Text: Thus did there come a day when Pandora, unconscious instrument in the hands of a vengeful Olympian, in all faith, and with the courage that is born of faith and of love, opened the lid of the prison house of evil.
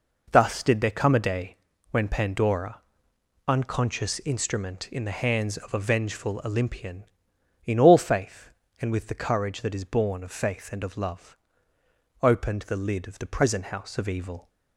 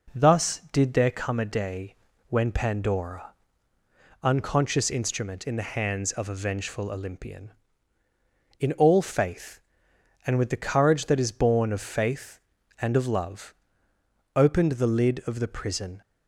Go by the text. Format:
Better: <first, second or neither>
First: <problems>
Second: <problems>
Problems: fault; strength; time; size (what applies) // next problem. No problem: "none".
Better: first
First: pauses between "day" and "when"; slight; at 1.5 s; 0.34 s long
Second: pauses between "day" and "when"; slight; at 1.9 s; 0.34 s long // stops before "house of evil"; at 16.0 s